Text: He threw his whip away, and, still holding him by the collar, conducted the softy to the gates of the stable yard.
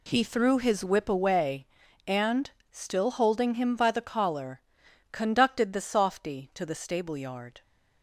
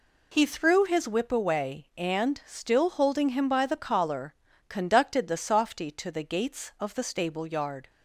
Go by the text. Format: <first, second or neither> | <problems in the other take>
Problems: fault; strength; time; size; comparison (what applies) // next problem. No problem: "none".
second | skips "gates of the"; at 6.7 s